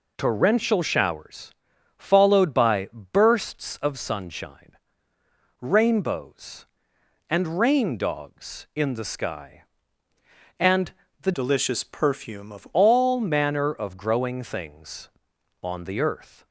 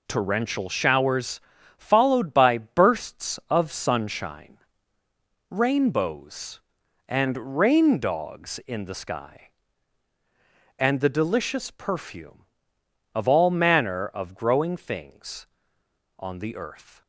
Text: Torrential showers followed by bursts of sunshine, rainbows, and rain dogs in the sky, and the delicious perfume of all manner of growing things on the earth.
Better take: second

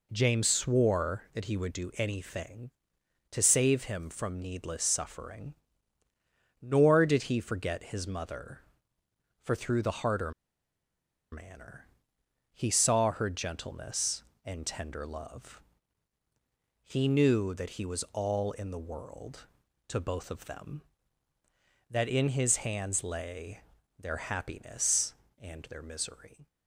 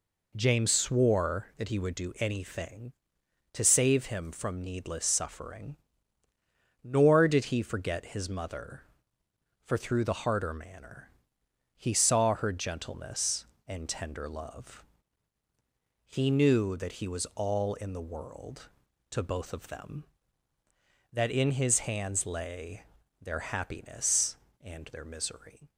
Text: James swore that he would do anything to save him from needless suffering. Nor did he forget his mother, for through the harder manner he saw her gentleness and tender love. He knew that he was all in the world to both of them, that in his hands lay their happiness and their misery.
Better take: second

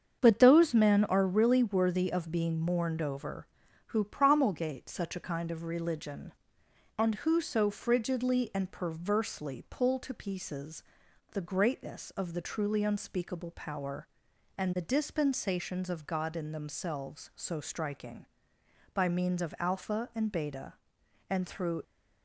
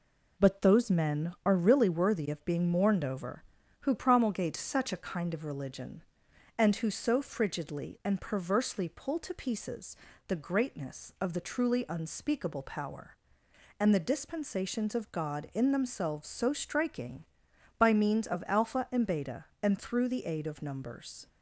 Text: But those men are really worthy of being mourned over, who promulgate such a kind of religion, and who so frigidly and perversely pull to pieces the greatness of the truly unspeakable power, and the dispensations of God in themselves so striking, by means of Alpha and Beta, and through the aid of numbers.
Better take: second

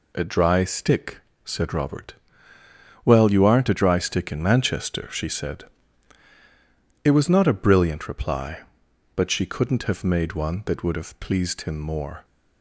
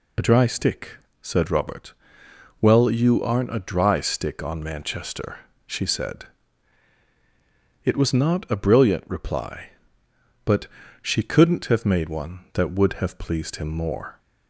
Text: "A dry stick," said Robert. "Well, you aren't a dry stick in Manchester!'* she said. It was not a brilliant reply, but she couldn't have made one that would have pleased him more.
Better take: first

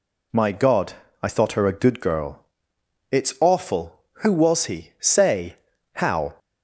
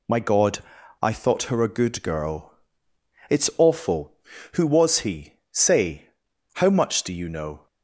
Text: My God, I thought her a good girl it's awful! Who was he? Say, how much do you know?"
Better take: second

